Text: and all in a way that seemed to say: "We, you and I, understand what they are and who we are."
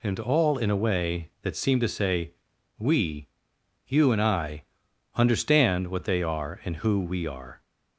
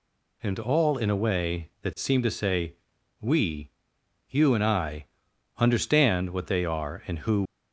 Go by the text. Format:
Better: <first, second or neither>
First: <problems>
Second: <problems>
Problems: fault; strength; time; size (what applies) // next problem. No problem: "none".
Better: first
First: none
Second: stops before "we are"; at 7.4 s